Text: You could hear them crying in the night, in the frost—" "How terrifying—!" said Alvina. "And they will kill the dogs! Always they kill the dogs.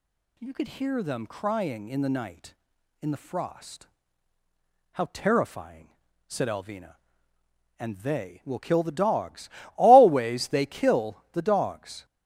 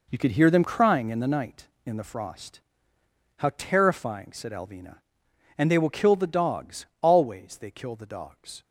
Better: first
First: none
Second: gets quieter; strong; throughout; 9.5 dB

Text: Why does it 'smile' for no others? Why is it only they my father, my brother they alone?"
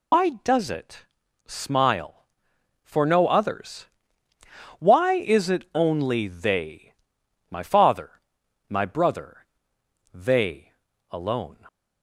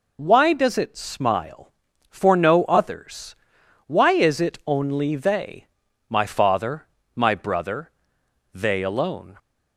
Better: second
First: loses the start of "Why"; at 0.1 s; 80 ms // pauses between "it" and "smile"; at 1.0 s; 0.42 s long // pauses between "they" and "my"; noticeable; at 6.9 s; 0.56 s long // pauses between "brother" and "they"; noticeable; at 9.4 s; 0.70 s long // pauses between "they" and "alone"; at 10.7 s; 0.38 s long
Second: pauses between "they" and "my"; noticeable; at 5.6 s; 0.46 s long // pauses between "brother" and "they"; noticeable; at 7.8 s; 0.62 s long

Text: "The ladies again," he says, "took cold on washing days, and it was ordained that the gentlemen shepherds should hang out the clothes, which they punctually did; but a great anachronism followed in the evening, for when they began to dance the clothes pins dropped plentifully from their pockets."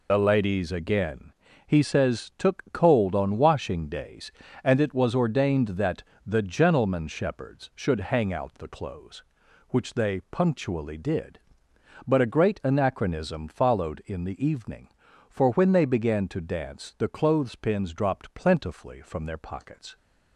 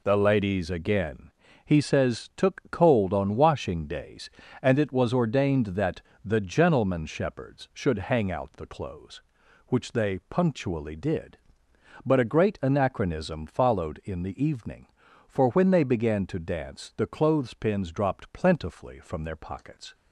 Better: second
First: loses the start of "The"; at 0.0 s; 40 ms // pauses between "that" and "the"; slight; at 6.0 s; 0.22 s long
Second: pauses between "that" and "the"; slight; at 6.0 s; 0.22 s long

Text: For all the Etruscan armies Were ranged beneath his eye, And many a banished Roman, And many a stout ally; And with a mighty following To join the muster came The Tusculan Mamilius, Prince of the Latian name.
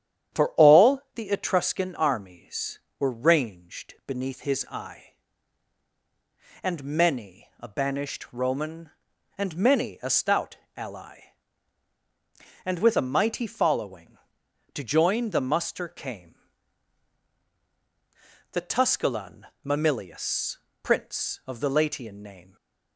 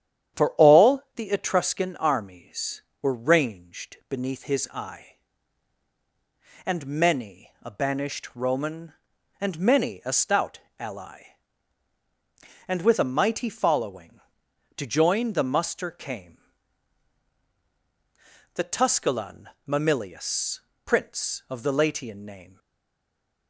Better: first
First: starts louder than the rest; strong; until 1.5 s; 10 dB // pauses between "stout" and "ally"; slight; at 10.5 s; 0.22 s long // pauses between "came" and "The"; strong; at 16.3 s; 2.1 s long // pauses between "Tusculan" and "Mamilius"; slight; at 19.4 s; 0.20 s long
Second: starts louder than the rest; strong; until 1.5 s; 10 dB // pauses between "stout" and "ally"; slight; at 10.5 s; 0.22 s long // pauses between "came" and "The"; strong; at 16.3 s; 2.1 s long // pauses between "Tusculan" and "Mamilius"; slight; at 19.4 s; 0.20 s long // stays silent after the last word; slight; from 22.5 s on; 0.9 s long

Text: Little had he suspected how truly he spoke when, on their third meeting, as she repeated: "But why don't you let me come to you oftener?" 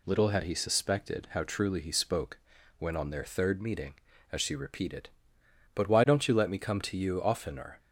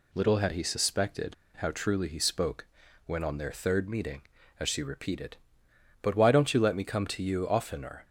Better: first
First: pauses between "spoke" and "when"; at 2.3 s; 0.40 s long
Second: pauses between "suspected" and "how"; slight; at 1.3 s; 0.23 s long // pauses between "spoke" and "when"; at 2.6 s; 0.40 s long

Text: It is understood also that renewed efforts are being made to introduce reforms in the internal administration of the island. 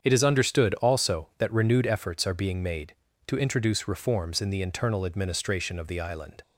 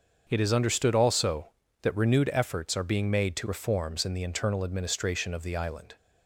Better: first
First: starts louder than the rest; strong; until 1.0 s; 7.5 dB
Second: starts louder than the rest; until 1.3 s; 6.5 dB // skips "introduce"; at 3.4 s

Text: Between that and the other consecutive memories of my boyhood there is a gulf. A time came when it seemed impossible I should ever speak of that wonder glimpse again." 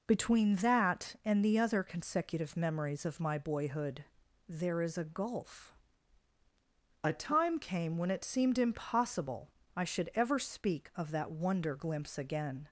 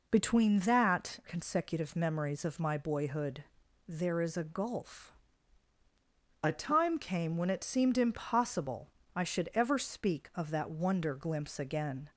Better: first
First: pauses between "boyhood" and "there"; at 4.0 s; 0.44 s long // pauses between "impossible" and "I"; slight; at 9.4 s; 0.26 s long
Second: skips "and the other"; at 1.2 s // pauses between "boyhood" and "there"; at 3.4 s; 0.44 s long // pauses between "impossible" and "I"; slight; at 8.8 s; 0.26 s long

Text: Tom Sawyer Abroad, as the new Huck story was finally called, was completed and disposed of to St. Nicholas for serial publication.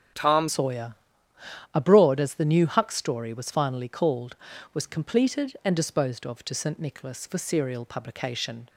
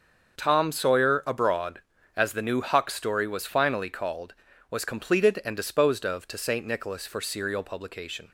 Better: second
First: starts louder than the rest; strong; until 1.9 s; 7.5 dB // changes voice at "Sawyer"; from 0.4 s on; 8.2 s long // pauses between "Sawyer" and "Abroad"; noticeable; at 0.9 s; 0.78 s long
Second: starts louder than the rest; until 1.4 s; 6.5 dB

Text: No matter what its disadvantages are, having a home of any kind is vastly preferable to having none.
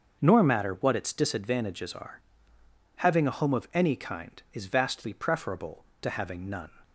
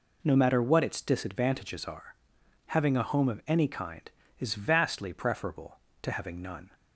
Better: second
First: starts louder than the rest; until 1.2 s; 6.5 dB // says "Nor" for "No"; at 0.2 s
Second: none

